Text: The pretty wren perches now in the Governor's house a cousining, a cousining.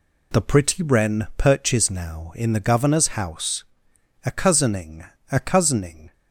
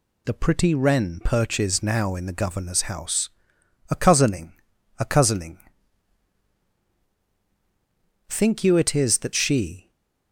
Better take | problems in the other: first | pauses between "house" and "a"; noticeable; at 3.3 s; 0.58 s long; noticeable in the first // goes on to say "Think you it is that she"; from 8.2 s on; 1.6 s long // stays silent after the last word; slight; from 9.8 s on; 0.5 s long

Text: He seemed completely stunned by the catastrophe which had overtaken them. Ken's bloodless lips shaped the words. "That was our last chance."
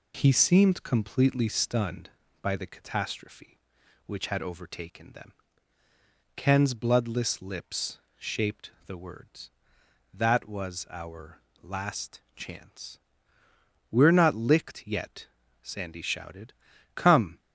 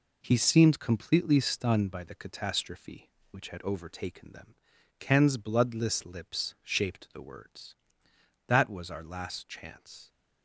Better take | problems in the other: second | pauses between "lips" and "shaped"; slight; at 7.9 s; 0.20 s long // pauses between "our" and "last"; slight; at 11.4 s; 0.19 s long // pauses between "last" and "chance"; slight; at 12.2 s; 0.16 s long // goes on to say "We're not licked yet Sandy shouted Come"; strong; from 13.9 s on; 3.4 s long

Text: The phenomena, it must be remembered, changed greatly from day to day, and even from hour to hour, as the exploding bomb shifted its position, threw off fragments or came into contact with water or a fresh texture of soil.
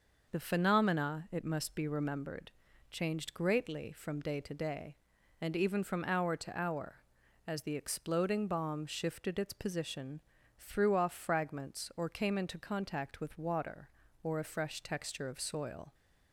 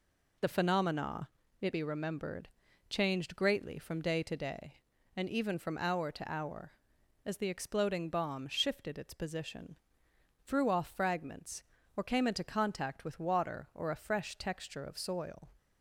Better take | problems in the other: first | skips "must"; at 1.7 s

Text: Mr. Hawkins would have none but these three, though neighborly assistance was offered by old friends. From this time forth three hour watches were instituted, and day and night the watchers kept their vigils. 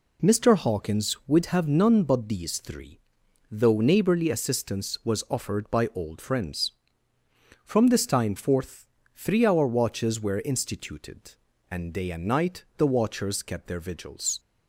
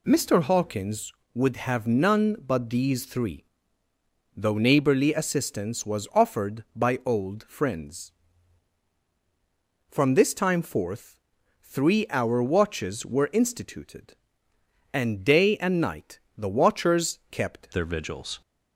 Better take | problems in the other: first | pauses between "forth" and "three"; noticeable; at 11.1 s; 0.46 s long; slight in the first // pauses between "night" and "the"; slight; at 16.1 s; 0.18 s long // changes voice at "their"; from 17.7 s on; 0.7 s long

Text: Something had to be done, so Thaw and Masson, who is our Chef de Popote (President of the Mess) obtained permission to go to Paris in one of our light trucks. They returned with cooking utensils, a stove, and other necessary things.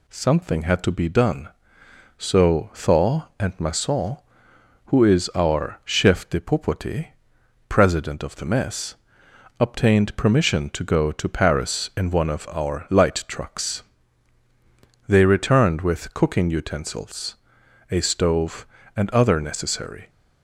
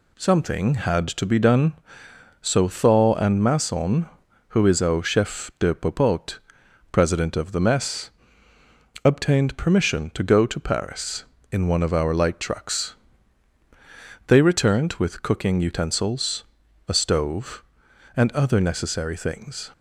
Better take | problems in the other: second | stops before "things"; at 20.0 s

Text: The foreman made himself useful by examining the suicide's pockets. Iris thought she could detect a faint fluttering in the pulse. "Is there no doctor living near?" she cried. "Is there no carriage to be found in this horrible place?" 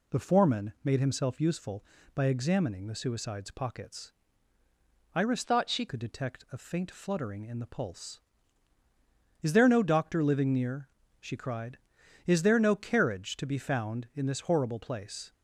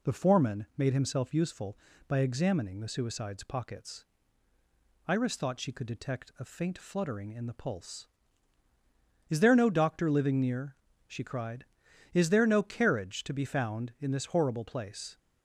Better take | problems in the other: second | changes voice from "thought" to "she"; from 5.4 to 5.8 s; 0.4 s long

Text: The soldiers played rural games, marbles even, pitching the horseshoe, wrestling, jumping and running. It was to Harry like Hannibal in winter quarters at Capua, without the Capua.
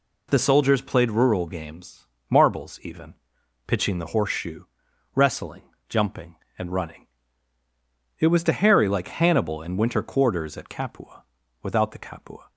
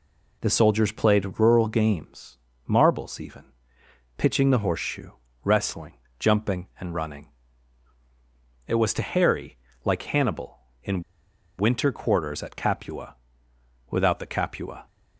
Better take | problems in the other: first | pauses between "Harry" and "like"; slight; at 9.5 s; 0.26 s long // pauses between "in" and "winter"; noticeable; at 11.0 s; 0.57 s long

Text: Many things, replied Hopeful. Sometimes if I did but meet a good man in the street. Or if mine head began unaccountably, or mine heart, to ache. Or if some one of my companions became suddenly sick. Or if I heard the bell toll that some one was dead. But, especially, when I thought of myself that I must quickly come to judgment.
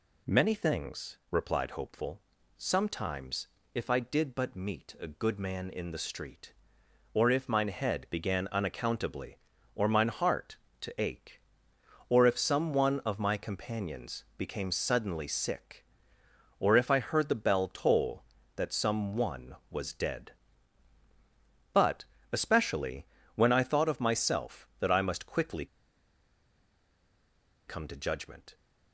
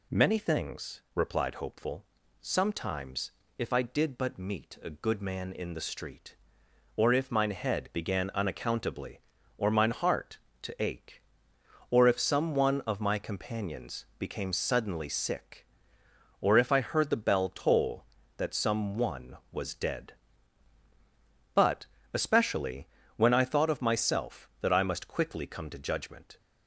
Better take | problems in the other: second | pauses between "Sometimes" and "if"; slight; at 3.4 s; 0.30 s long; slight in the second // pauses between "quickly" and "come"; strong; at 25.6 s; 2.0 s long

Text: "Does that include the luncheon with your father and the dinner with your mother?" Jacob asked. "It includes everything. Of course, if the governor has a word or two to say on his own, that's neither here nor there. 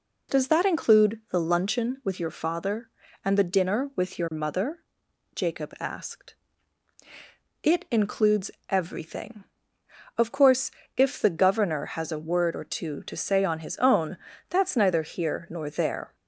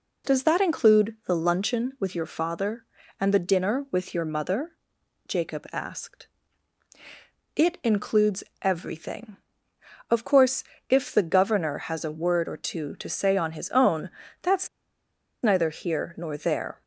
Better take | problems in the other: first | pauses between "includes" and "everything"; slight; at 8.4 s; 0.22 s long; slight in the first // pauses between "that's" and "neither"; noticeable; at 14.6 s; 0.75 s long

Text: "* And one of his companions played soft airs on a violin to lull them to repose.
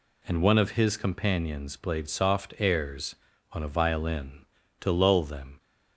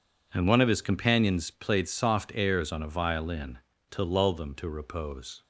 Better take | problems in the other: second | stops before "to repose"; at 5.5 s

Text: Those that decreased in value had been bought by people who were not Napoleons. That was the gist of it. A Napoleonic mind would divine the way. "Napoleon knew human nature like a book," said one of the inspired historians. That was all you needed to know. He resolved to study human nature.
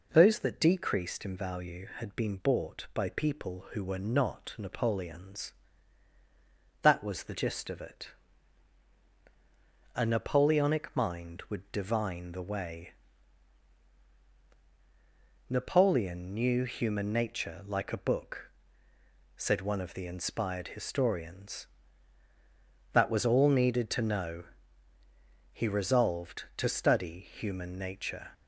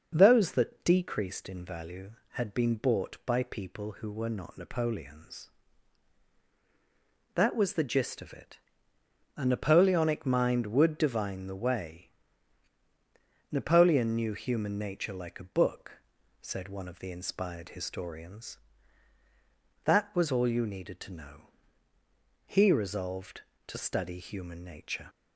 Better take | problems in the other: second | skips "you"; at 23.4 s

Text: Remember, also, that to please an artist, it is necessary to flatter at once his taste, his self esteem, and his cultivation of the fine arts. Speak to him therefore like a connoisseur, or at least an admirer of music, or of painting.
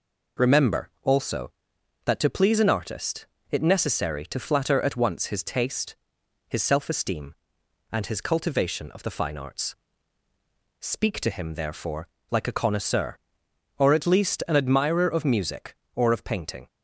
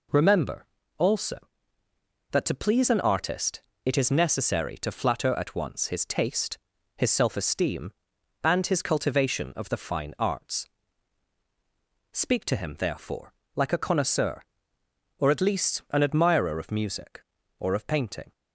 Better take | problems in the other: second | skips "is"; at 3.6 s // pauses between "therefore" and "like"; slight; at 12.0 s; 0.22 s long; slight in the second

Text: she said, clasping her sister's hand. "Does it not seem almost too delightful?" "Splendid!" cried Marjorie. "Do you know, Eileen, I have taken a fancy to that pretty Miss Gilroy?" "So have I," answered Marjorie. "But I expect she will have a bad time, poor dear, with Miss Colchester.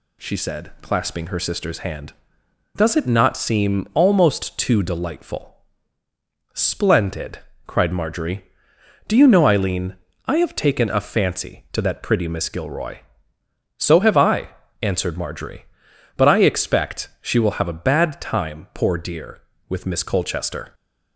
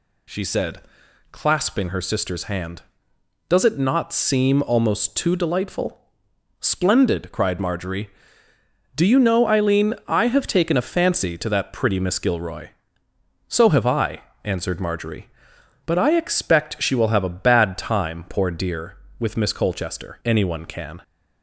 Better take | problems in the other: first | goes on to say "Anyone can"; noticeable; from 20.2 s on; 0.74 s long

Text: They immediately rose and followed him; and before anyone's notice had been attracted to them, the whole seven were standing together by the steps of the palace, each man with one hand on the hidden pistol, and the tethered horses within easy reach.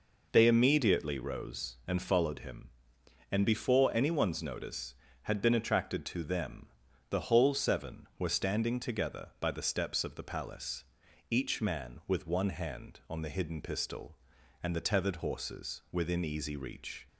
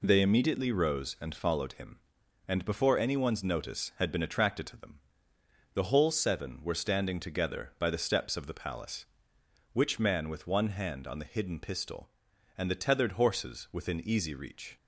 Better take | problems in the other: first | says "which" for "each"; at 9.7 s

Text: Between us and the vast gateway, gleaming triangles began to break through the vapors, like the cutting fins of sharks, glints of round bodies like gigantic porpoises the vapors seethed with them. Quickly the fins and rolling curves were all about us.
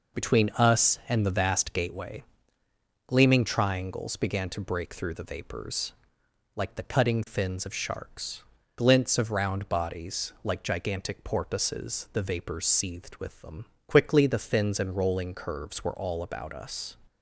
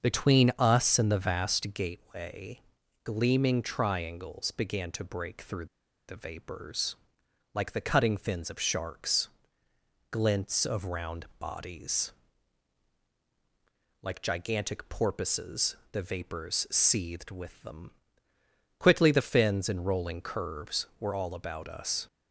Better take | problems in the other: first | starts louder than the rest; until 1.0 s; 6.5 dB // pauses between "through" and "the"; at 5.6 s; 0.42 s long // pauses between "bodies" and "like"; strong; at 12.1 s; 1.9 s long // pauses between "porpoises" and "the"; slight; at 15.7 s; 0.16 s long

